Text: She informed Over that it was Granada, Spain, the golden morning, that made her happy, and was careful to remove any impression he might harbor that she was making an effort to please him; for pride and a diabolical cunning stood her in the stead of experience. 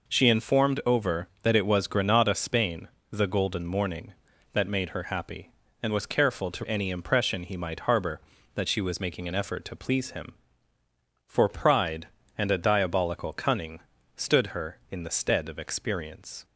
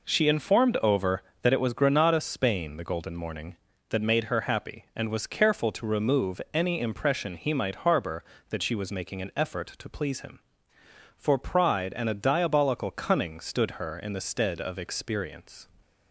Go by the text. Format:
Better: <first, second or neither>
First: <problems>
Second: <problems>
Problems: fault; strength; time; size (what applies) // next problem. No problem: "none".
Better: second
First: skips "remove"; at 6.6 s // pauses between "cunning" and "stood"; slight; at 13.8 s; 0.34 s long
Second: none